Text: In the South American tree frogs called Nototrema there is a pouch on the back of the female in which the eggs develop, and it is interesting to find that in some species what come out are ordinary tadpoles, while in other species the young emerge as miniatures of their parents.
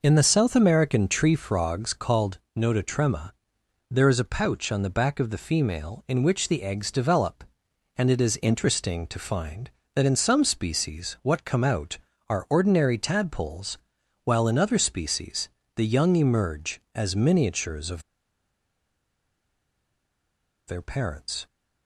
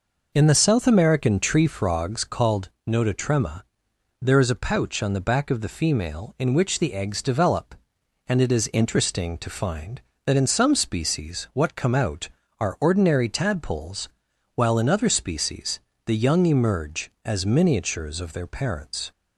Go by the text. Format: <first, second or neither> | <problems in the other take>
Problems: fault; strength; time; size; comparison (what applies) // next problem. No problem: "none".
second | pauses between "called" and "Nototrema"; slight; at 2.3 s; 0.18 s long; slight in the second // pauses between "Nototrema" and "there"; noticeable; at 3.3 s; 0.58 s long; noticeable in the second // pauses between "species" and "the"; slight; at 15.4 s; 0.26 s long; slight in the second // pauses between "of" and "their"; strong; at 18.0 s; 2.6 s long